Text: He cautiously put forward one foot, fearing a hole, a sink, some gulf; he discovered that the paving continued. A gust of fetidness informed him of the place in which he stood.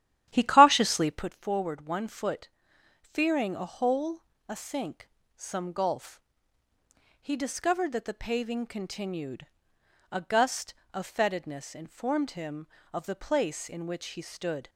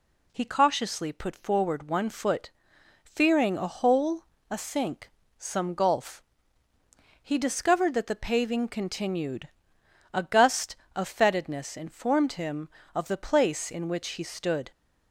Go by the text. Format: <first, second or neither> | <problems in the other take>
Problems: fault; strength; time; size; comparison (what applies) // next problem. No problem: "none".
second | starts louder than the rest; strong; until 1.3 s; 11.5 dB